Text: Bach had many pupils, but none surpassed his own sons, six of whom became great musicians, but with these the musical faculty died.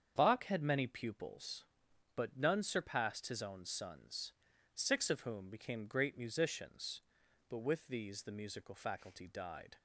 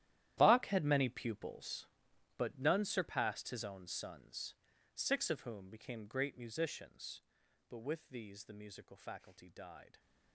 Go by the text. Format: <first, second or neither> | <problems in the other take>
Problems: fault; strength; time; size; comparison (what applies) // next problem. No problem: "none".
first | gets quieter; strong; throughout; 16.5 dB // starts louder than the rest; strong; until 1.3 s; 12.5 dB; strong in the first